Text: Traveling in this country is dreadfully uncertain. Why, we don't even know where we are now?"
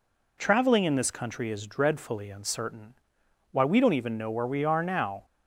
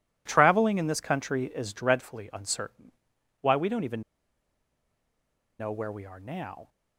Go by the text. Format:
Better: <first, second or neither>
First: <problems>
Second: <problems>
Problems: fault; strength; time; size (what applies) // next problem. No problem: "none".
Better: first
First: none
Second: pauses between "even" and "know"; strong; at 4.0 s; 1.5 s long